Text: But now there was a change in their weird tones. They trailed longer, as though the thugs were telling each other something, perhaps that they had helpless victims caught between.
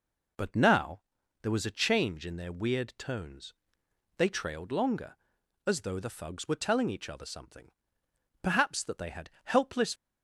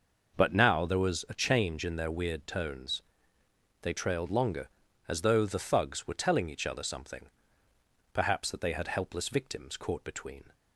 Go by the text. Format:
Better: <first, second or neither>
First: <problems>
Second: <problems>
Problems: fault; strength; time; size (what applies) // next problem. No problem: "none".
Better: second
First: pauses between "now" and "there"; at 1.0 s; 0.42 s long // pauses between "had" and "helpless"; slight; at 9.2 s; 0.16 s long // stops before "victims caught between"; at 9.9 s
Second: none